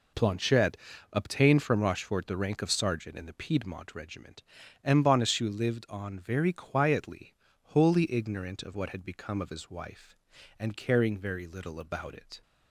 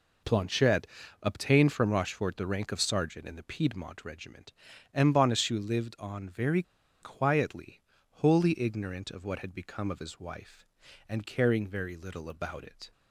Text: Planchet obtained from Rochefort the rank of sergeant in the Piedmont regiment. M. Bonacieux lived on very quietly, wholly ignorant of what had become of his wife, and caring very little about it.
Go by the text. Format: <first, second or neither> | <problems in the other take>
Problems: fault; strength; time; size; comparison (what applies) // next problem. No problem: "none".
first | pauses between "Planchet" and "obtained"; slight; at 0.8 s; 0.36 s long; slight in the first // pauses between "very" and "quietly"; at 6.6 s; 0.40 s long